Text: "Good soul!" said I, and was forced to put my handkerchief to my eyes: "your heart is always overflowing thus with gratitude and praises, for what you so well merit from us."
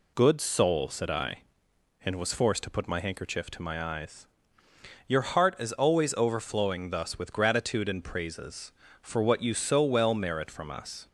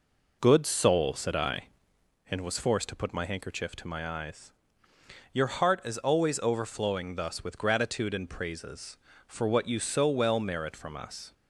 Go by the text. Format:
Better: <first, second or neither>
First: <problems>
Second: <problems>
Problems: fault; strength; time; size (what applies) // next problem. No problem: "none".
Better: first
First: none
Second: starts louder than the rest; noticeable; until 2.2 s; 4.5 dB